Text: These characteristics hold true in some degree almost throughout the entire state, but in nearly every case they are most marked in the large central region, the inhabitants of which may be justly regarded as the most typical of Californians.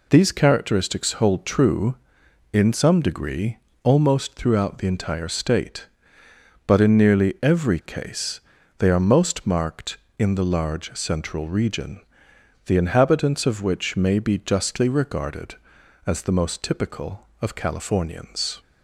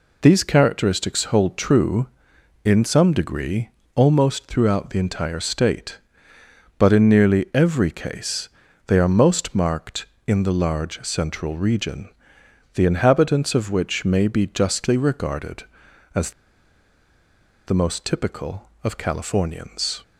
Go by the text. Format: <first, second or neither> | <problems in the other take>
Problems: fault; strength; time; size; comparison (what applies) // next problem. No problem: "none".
first | pauses between "degree" and "almost"; slight; at 3.6 s; 0.26 s long; slight in the first // pauses between "case" and "they"; at 8.4 s; 0.38 s long; also in the first // pauses between "as" and "the"; strong; at 16.3 s; 1.3 s long